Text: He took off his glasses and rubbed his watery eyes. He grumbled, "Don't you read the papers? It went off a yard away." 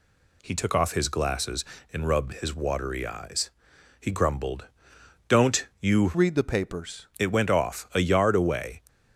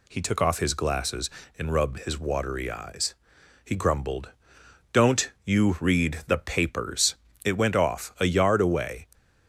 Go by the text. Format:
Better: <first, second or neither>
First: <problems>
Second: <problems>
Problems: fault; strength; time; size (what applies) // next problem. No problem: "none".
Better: second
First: pauses between "Don't" and "you"; slight; at 5.6 s; 0.16 s long // changes voice from "read" to "papers"; from 6.1 to 7.0 s; 0.9 s long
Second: pauses between "Don't" and "you"; slight; at 5.2 s; 0.16 s long